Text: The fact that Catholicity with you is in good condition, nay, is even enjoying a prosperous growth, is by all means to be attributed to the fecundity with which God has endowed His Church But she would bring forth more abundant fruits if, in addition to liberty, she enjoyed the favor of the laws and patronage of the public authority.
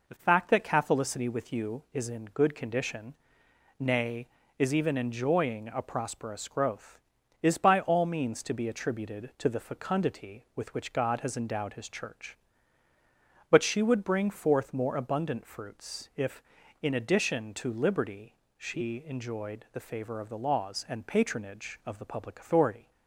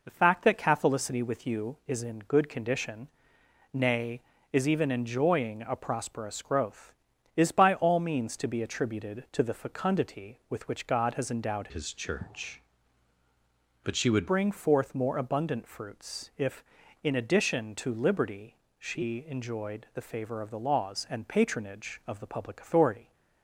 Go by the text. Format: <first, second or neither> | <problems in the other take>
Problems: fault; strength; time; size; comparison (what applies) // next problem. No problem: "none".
first | changes voice from "His" to "would"; from 11.7 to 14.2 s; 2.5 s long